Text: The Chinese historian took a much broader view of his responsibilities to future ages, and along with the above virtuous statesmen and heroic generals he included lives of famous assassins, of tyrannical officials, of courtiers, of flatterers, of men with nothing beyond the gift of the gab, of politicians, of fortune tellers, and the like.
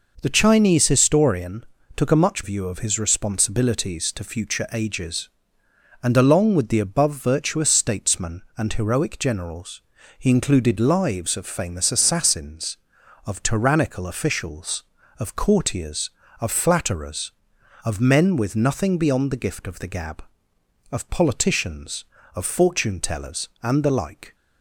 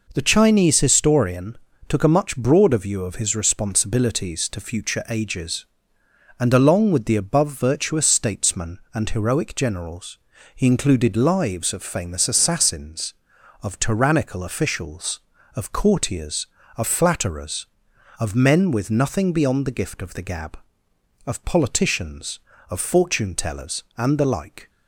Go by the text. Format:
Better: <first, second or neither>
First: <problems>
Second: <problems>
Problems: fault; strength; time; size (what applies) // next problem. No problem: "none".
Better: second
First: pauses between "historian" and "took"; slight; at 1.6 s; 0.30 s long // skips "broader"; at 2.4 s // pauses between "generals" and "he"; at 9.8 s; 0.38 s long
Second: pauses between "historian" and "took"; slight; at 1.5 s; 0.30 s long // pauses between "generals" and "he"; at 10.1 s; 0.38 s long